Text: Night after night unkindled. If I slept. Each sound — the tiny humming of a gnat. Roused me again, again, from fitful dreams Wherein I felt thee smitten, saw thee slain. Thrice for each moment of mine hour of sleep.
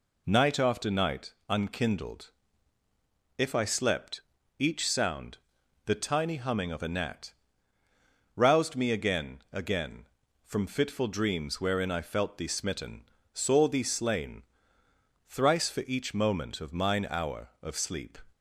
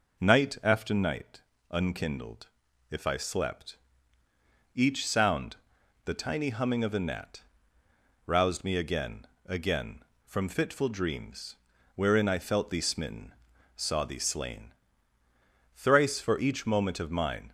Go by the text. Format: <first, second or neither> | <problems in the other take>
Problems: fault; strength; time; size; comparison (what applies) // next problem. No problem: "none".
first | pauses between "night" and "unkindled"; slight; at 1.4 s; 0.28 s long; slight in the first // pauses between "dreams" and "Wherein"; at 11.5 s; 0.38 s long // stops before "hour of sleep"; at 17.4 s